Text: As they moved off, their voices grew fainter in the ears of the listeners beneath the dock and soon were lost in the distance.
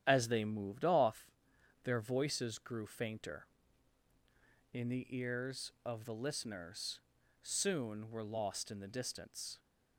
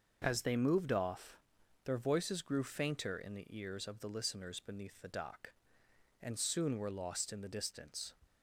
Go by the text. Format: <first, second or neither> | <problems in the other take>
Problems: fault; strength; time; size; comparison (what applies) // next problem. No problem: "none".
second | starts louder than the rest; strong; until 1.0 s; 10 dB; also in the second // skips "beneath the dock and"; at 7.1 s